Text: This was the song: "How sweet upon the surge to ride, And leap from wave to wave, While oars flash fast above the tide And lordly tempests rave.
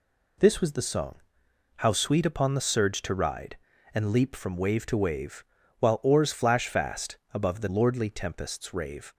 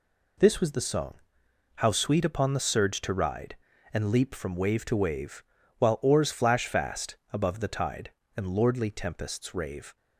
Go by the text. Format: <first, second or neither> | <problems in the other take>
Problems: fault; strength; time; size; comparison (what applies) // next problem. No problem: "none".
second | pauses between "fast" and "above"; slight; at 7.1 s; 0.16 s long; slight in the second // skips "tide And"; at 7.6 s